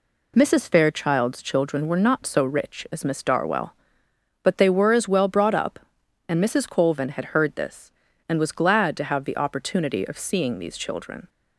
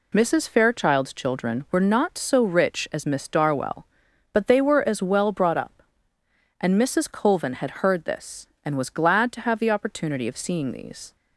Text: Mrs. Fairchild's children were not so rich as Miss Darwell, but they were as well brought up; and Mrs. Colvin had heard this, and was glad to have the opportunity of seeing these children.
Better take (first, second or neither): first